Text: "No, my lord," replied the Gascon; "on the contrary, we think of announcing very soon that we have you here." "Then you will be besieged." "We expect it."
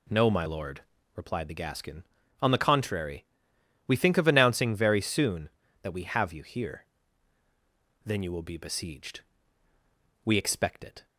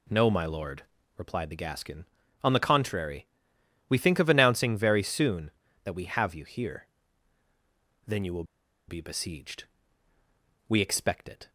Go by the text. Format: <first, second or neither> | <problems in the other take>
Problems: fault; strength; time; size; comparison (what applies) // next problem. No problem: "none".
first | pauses between "will" and "be"; at 8.4 s; 0.44 s long